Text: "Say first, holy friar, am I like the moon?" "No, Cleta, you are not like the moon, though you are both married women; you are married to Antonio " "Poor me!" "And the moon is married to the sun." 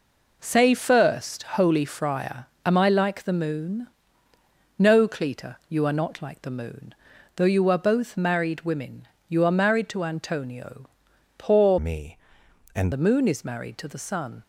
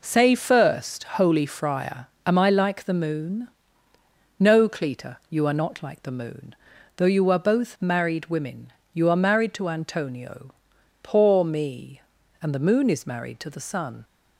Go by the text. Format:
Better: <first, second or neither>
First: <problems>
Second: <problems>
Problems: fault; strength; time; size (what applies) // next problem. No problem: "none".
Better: second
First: changes voice from "me" to "And"; from 11.7 to 12.9 s; 1.2 s long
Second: none